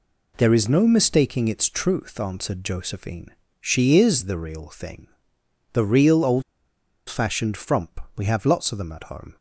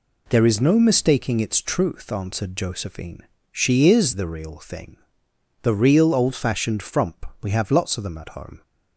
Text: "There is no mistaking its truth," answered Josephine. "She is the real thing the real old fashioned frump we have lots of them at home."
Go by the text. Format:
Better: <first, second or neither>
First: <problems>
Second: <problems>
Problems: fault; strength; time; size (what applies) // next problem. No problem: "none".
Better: second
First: pauses between "thing" and "the"; noticeable; at 5.0 s; 0.64 s long // pauses between "old" and "fashioned"; noticeable; at 6.4 s; 0.66 s long // pauses between "frump" and "we"; slight; at 8.0 s; 0.16 s long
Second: pauses between "thing" and "the"; noticeable; at 4.9 s; 0.64 s long // pauses between "frump" and "we"; slight; at 7.2 s; 0.16 s long